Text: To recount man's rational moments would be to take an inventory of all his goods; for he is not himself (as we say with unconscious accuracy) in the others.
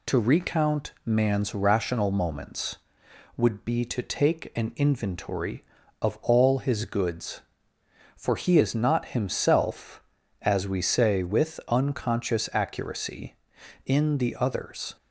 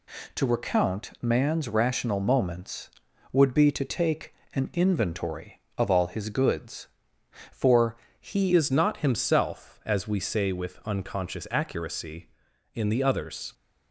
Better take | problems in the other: first | pauses between "take" and "an"; slight; at 4.3 s; 0.22 s long // pauses between "for" and "he"; slight; at 7.9 s; 0.24 s long // changes voice at "is"; from 8.5 s on; 5.0 s long

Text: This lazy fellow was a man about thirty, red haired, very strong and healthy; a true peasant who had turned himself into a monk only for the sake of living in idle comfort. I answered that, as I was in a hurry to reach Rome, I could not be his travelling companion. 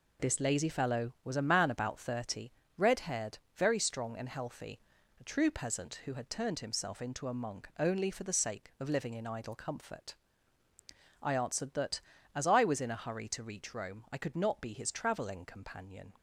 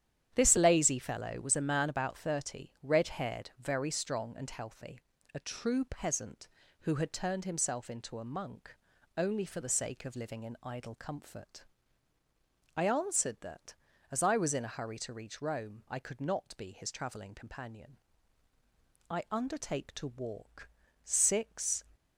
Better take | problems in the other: first | starts louder than the rest; strong; until 1.3 s; 10 dB // pauses between "monk" and "only"; at 8.7 s; 0.38 s long // goes on to say "I undertake to walk six"; strong; from 19.1 s on; 2.7 s long

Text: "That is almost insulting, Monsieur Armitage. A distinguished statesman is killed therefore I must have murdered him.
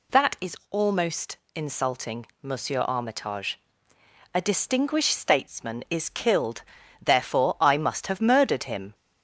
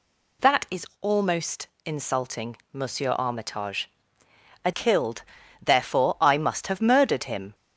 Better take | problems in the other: first | pauses between "is" and "almost"; slight; at 0.8 s; 0.16 s long; slight in the first // pauses between "almost" and "insulting"; slight; at 1.6 s; 0.18 s long; slight in the first // skips "distinguished statesman is"; at 4.7 s // pauses between "killed" and "therefore"; slight; at 5.2 s; 0.36 s long; slight in the first

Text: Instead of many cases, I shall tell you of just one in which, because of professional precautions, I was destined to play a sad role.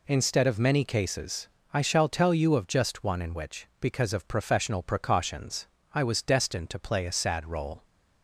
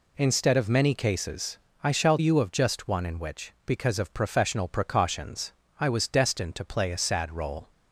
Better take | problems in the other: first | skips "tell"; at 2.1 s

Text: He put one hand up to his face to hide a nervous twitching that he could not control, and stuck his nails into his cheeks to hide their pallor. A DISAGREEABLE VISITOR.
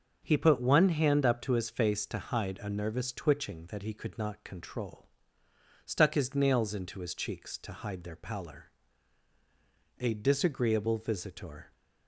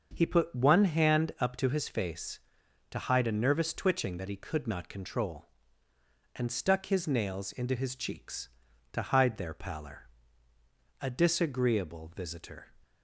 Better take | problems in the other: second | starts louder than the rest; until 1.2 s; 6.5 dB; also in the second // skips "and"; at 5.4 s

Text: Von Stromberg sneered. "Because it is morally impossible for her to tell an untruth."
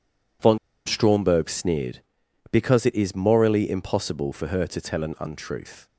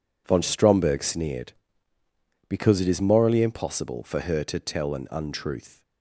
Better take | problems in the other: second | pauses between "Von" and "Stromberg"; slight; at 0.5 s; 0.28 s long

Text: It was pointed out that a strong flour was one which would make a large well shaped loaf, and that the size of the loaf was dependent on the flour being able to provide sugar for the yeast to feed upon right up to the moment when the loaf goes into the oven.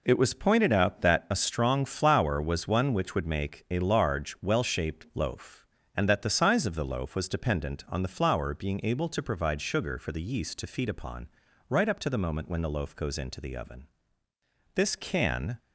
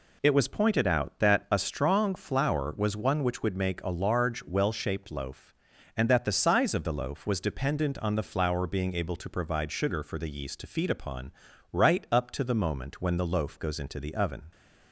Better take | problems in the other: second | pauses between "upon" and "right"; at 11.2 s; 0.42 s long; also in the second // goes on to say "This can"; noticeable; from 14.7 s on; 0.84 s long

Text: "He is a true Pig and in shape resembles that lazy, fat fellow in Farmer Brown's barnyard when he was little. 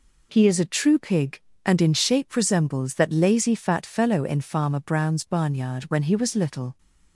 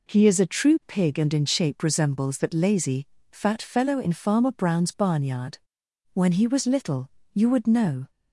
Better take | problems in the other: first | pauses between "barnyard" and "when"; noticeable; at 5.5 s; 0.54 s long // goes on to say "You would know"; noticeable; from 7.3 s on; 0.78 s long

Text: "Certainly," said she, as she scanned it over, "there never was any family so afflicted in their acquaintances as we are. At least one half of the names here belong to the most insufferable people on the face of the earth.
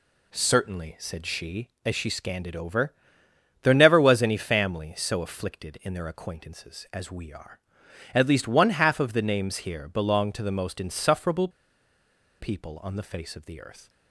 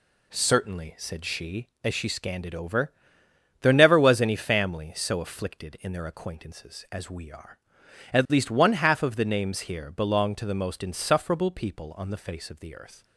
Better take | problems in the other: second | pauses between "insufferable" and "people"; noticeable; at 11.4 s; 0.91 s long

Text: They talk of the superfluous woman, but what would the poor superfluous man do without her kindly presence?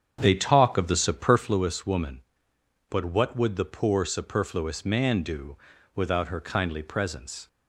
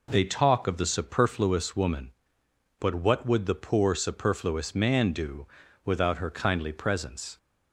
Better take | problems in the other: second | starts louder than the rest; strong; until 1.6 s; 8 dB // pauses between "do" and "without"; at 5.5 s; 0.40 s long; also in the second

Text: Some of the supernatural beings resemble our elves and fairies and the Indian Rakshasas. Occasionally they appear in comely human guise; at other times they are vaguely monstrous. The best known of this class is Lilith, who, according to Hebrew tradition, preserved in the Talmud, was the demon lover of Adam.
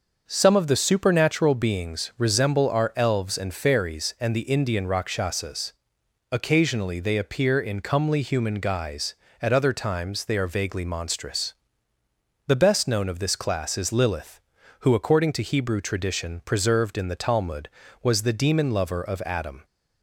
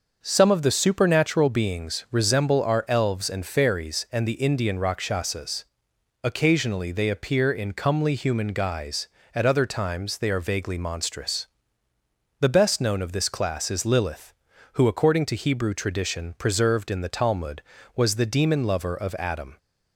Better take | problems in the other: neither | starts louder than the rest; the same in both

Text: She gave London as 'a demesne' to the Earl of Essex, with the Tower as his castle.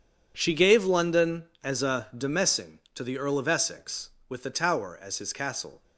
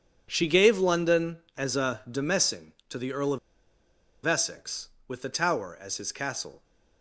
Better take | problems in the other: first | pauses between "of" and "Essex"; noticeable; at 3.3 s; 0.86 s long

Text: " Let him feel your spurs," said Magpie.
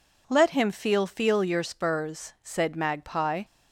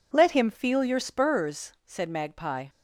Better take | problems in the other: second | says "feel" twice; at 1.0 s

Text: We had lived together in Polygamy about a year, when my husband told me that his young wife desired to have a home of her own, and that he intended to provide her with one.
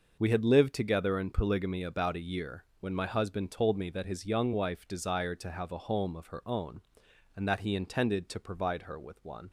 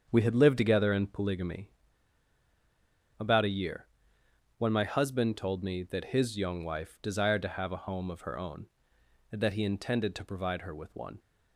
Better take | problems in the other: first | starts louder than the rest; strong; until 1.1 s; 7.5 dB // pauses between "Polygamy" and "about"; strong; at 1.6 s; 1.4 s long

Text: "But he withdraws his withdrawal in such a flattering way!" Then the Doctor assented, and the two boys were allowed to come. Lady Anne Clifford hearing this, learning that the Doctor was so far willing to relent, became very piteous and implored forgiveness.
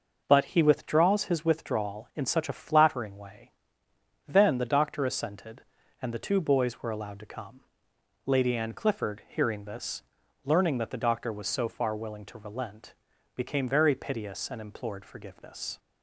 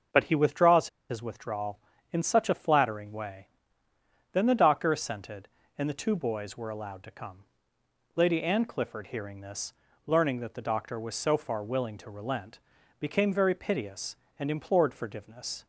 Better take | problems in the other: first | starts louder than the rest; until 1.3 s; 6.5 dB // pauses between "withdraws" and "his"; slight; at 0.8 s; 0.22 s long

